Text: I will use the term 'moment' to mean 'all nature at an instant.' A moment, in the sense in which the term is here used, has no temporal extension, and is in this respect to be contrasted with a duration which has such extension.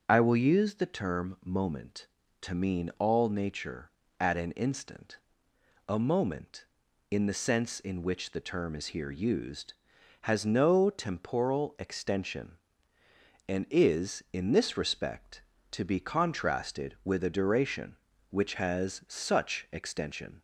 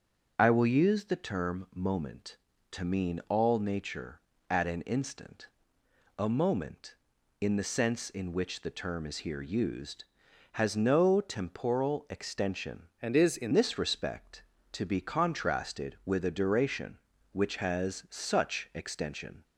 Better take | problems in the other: first | starts louder than the rest; until 1.3 s; 7 dB; also in the first // changes voice from "and" to "in"; from 13.0 to 13.5 s; 0.5 s long

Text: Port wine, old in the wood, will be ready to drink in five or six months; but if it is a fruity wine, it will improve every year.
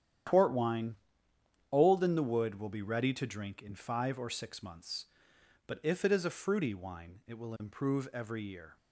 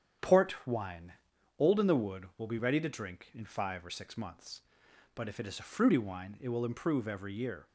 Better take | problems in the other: neither | starts louder than the rest; strong; the same in both

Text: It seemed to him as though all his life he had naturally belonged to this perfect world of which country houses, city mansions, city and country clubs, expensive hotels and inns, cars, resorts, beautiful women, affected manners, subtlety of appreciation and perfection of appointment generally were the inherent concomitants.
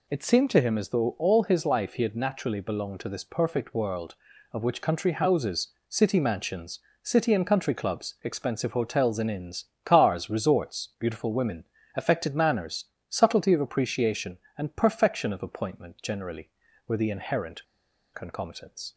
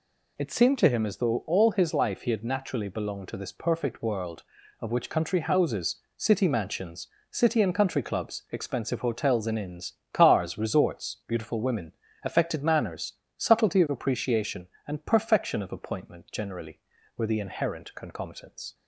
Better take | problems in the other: second | pauses between "inherent" and "concomitants"; noticeable; at 17.6 s; 0.49 s long

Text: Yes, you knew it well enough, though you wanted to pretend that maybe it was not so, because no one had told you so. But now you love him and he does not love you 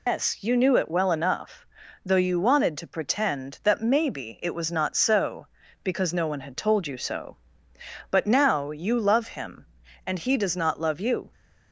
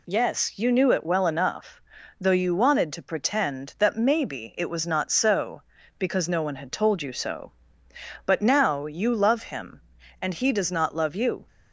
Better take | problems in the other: second | loses the start of "Yes"; at 0.0 s; 150 ms

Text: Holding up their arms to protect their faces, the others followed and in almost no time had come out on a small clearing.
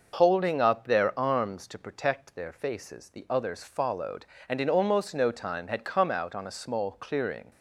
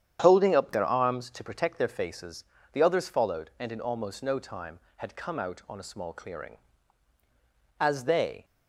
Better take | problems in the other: first | starts louder than the rest; strong; until 1.2 s; 9.5 dB // goes on to say "As they"; noticeable; from 7.8 s on; 0.64 s long

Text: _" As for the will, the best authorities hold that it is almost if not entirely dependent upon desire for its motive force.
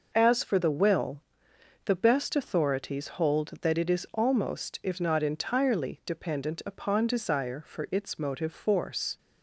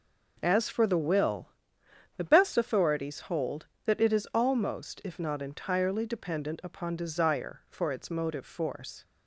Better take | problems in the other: neither | none

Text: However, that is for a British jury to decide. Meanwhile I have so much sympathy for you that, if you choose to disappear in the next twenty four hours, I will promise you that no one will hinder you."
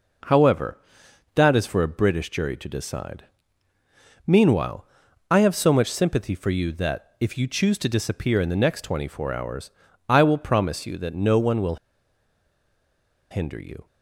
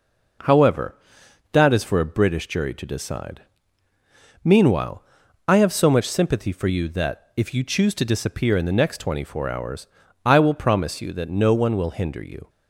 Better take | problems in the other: second | pauses between "Meanwhile" and "I"; at 4.8 s; 0.44 s long; also in the second // pauses between "will" and "hinder"; strong; at 11.7 s; 1.5 s long

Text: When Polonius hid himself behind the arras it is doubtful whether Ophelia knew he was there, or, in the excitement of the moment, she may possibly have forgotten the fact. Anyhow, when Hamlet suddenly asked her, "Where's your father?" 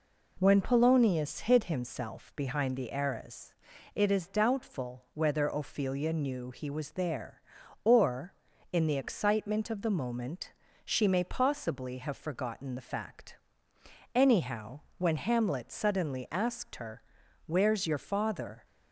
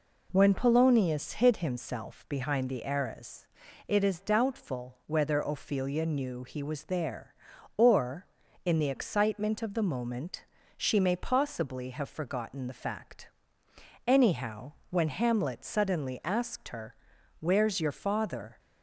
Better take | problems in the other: neither | pauses between "arras" and "it"; the same in both

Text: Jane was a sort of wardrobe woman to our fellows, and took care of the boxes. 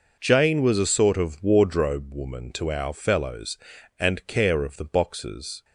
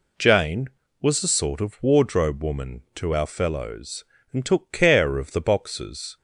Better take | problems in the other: second | skips "took"; at 4.2 s

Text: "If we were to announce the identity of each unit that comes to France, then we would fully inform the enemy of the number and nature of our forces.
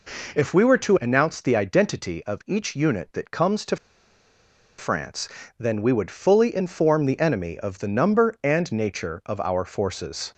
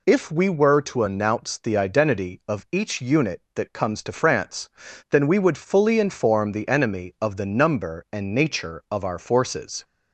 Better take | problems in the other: second | pauses between "to" and "France"; at 3.7 s; 1.0 s long

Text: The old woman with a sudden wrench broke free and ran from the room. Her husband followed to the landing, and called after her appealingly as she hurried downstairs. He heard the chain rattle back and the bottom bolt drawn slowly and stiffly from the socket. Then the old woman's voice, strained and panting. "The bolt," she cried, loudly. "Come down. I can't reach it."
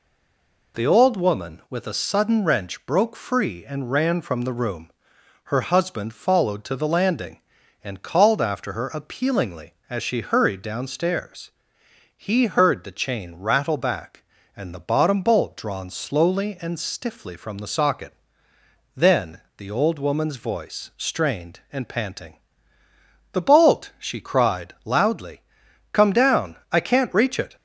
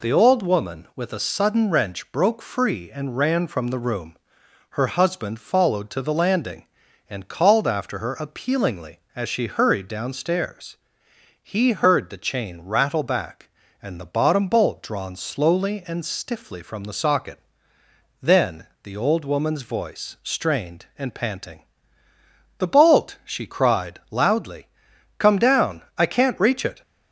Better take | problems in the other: second | stays silent before the first word; slight; until 0.7 s; 0.7 s long // pauses between "Then" and "the"; slight; at 19.4 s; 0.16 s long; slight in the second

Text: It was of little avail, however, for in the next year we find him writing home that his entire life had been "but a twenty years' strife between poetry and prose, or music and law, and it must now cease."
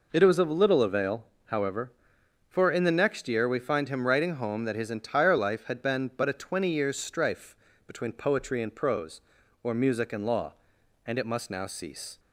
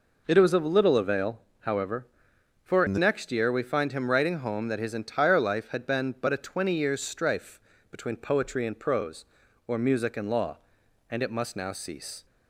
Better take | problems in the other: first | changes voice from "in" to "the"; from 2.8 to 2.9 s; 0.1 s long // pauses between "strife" and "between"; slight; at 7.5 s; 0.30 s long; slight in the first

